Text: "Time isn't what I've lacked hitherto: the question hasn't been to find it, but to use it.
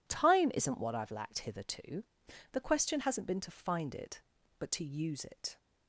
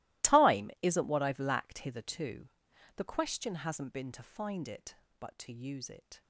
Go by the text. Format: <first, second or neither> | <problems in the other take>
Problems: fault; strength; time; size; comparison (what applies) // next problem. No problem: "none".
first | gets quieter; strong; throughout; 20 dB